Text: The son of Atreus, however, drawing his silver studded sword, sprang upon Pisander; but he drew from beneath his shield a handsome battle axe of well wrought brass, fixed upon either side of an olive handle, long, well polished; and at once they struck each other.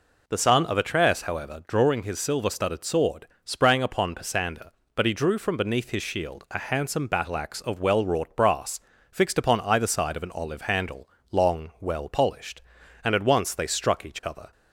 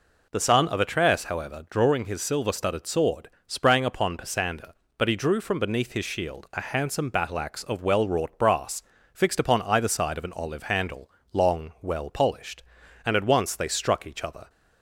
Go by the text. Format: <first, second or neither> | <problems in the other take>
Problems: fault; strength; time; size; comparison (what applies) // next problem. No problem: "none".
neither | none